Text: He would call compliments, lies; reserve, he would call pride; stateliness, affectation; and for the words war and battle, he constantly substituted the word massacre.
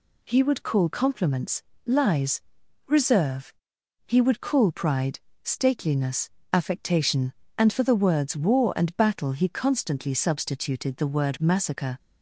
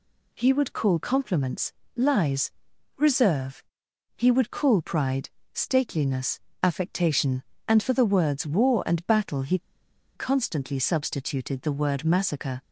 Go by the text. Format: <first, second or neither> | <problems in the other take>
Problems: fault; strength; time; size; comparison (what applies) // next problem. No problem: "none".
first | pauses between "he" and "constantly"; noticeable; at 9.5 s; 0.57 s long